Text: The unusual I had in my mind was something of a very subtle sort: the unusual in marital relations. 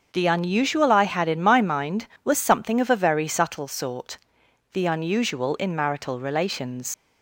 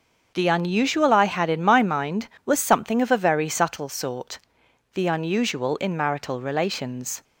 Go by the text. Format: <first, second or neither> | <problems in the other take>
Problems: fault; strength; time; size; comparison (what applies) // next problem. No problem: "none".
second | starts louder than the rest; until 1.1 s; 6.5 dB; also in the second // leaves "relations" unfinished; at 6.9 s; 80 ms